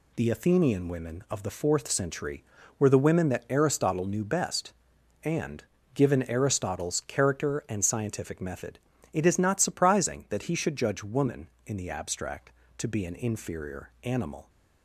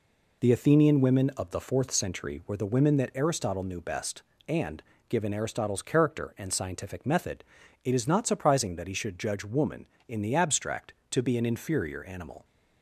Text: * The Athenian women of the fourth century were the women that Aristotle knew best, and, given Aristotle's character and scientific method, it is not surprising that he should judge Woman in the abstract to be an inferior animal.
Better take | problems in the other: neither | none

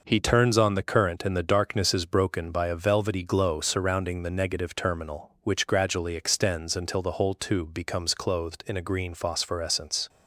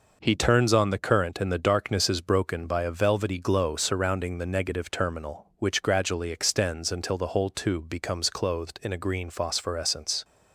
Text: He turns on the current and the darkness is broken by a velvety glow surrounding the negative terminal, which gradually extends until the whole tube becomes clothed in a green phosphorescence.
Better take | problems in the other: neither | none

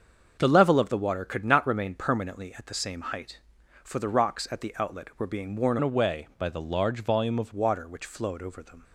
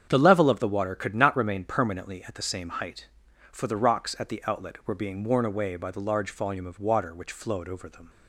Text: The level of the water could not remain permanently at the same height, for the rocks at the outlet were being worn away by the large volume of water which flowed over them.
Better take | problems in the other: second | starts louder than the rest; until 1.4 s; 6.5 dB; strong in the second // changes voice from "away" to "of"; from 5.8 to 7.5 s; 1.7 s long

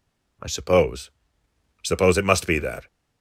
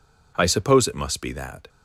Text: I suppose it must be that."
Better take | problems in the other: second | says "suppose" twice; at 1.8 s

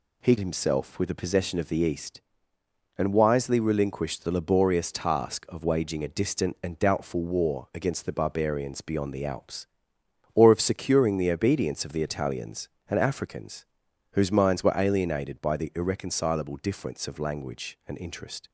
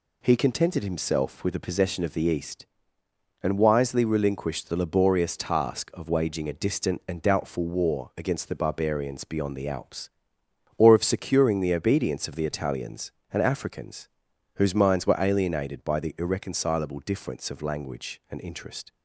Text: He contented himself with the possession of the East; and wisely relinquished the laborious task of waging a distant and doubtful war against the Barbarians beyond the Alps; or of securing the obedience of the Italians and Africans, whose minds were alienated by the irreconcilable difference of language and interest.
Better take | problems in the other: second | skips "contented"; at 0.3 s

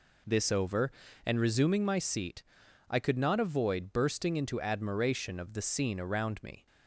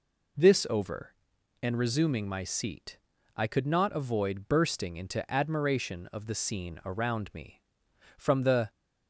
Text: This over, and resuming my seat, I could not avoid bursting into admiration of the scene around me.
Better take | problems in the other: first | goes on to say "From the"; from 8.1 s on; 0.52 s long

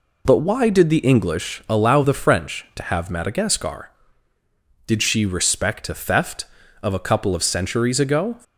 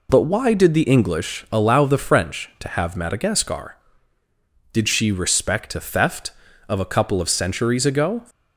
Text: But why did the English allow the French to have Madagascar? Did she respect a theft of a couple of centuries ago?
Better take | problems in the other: neither | none

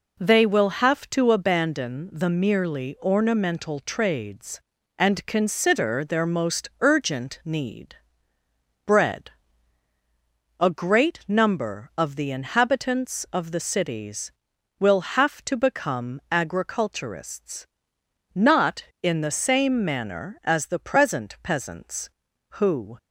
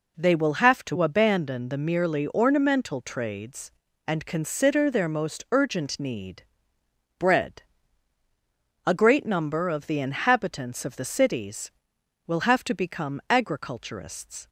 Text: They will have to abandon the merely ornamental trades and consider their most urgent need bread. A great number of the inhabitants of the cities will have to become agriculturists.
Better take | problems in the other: second | pauses between "need" and "bread"; noticeable; at 7.9 s; 0.90 s long; noticeable in the second // goes on to say "Not in the same manner as the present peasants who"; strong; from 18.3 s on; 4.6 s long

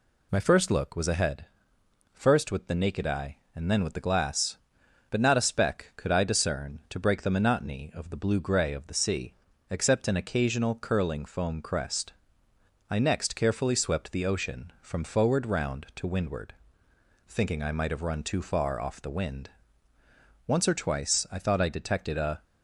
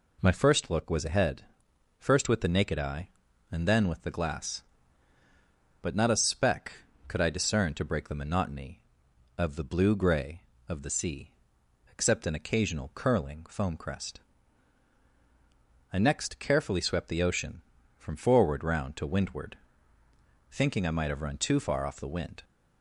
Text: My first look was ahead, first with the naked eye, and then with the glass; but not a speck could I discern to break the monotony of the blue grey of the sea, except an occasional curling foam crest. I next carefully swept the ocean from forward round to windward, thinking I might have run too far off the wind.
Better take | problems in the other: second | goes on to say "Once or twice I thought I detected a"; strong; from 20.4 s on; 1.9 s long

